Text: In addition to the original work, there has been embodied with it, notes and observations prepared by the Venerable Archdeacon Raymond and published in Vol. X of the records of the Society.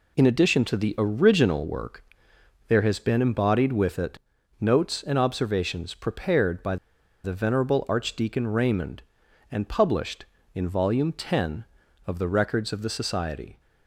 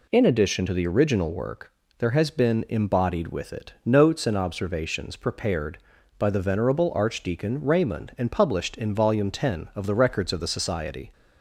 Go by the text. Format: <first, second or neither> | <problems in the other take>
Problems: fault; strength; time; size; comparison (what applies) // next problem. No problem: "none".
second | pauses between "by" and "the"; noticeable; at 6.7 s; 0.47 s long